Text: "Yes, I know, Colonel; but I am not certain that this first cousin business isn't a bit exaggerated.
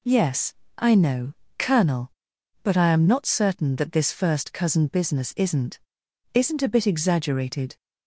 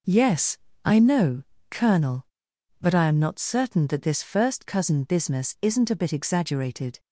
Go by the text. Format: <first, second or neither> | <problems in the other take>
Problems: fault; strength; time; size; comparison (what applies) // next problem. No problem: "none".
second | says "isn't" twice; at 6.3 s